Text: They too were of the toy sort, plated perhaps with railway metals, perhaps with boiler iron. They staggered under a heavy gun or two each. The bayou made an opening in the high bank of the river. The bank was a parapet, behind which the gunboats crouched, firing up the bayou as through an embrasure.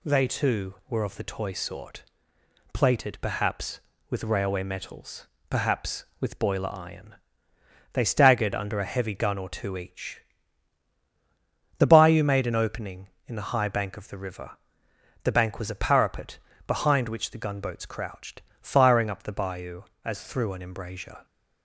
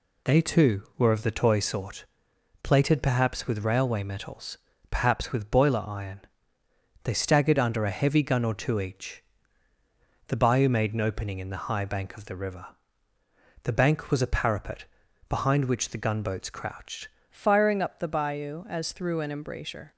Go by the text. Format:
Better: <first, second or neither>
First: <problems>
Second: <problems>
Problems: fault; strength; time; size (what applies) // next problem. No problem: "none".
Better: first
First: none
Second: changes voice at "firing"; from 17.3 s on; 2.6 s long